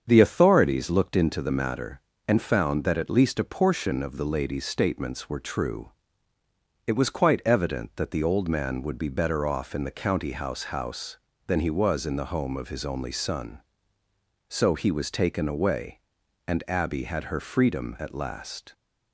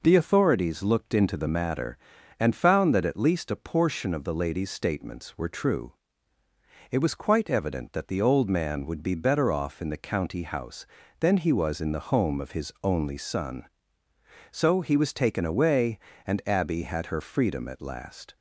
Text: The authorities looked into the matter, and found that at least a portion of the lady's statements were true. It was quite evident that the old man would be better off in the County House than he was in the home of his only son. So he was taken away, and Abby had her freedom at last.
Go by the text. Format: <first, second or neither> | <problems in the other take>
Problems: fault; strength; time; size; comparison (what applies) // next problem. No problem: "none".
second | starts louder than the rest; strong; until 1.0 s; 7 dB // says "House" twice; at 10.6 s